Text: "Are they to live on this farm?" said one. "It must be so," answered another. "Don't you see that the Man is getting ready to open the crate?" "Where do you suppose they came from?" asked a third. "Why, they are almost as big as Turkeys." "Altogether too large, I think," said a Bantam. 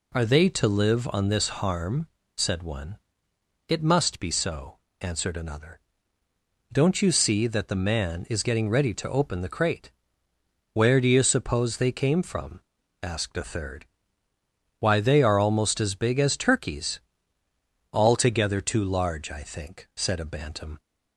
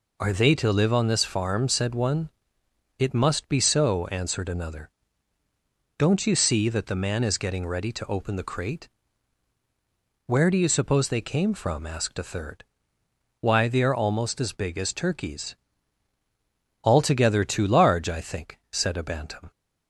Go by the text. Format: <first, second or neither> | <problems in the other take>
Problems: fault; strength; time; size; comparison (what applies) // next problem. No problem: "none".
second | says "harm" for "farm"; at 1.4 s